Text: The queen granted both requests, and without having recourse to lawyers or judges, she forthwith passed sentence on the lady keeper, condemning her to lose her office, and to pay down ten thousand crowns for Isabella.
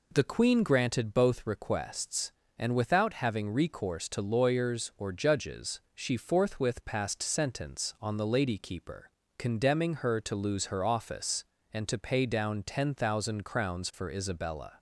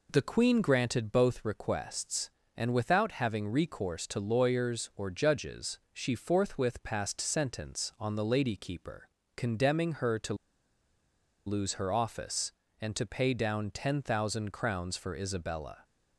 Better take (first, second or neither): first